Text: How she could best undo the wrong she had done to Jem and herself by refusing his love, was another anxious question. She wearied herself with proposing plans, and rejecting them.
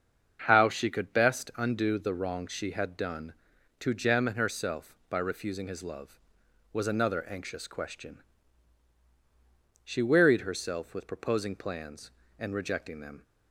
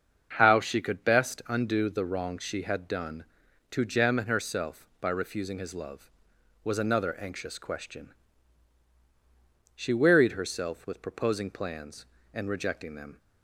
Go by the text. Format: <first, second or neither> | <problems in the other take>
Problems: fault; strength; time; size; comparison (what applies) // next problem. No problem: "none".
neither | starts louder than the rest; the same in both